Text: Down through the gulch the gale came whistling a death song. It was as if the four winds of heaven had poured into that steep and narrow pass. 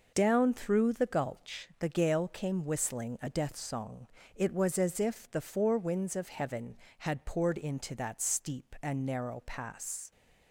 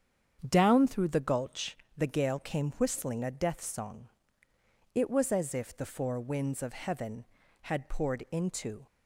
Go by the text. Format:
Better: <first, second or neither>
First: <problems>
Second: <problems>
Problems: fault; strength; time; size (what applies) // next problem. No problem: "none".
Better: first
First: none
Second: starts louder than the rest; strong; until 1.4 s; 8 dB // pauses between "gulch" and "the"; slight; at 1.7 s; 0.22 s long // stops before "that steep and narrow pass"; at 8.8 s